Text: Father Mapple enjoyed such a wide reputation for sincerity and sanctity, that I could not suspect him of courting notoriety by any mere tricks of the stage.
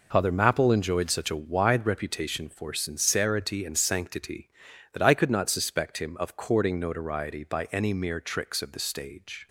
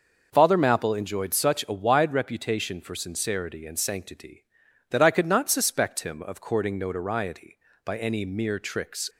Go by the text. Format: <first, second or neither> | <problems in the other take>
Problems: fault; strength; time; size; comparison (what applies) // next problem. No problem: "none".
first | stops before "of the stage"; at 9.1 s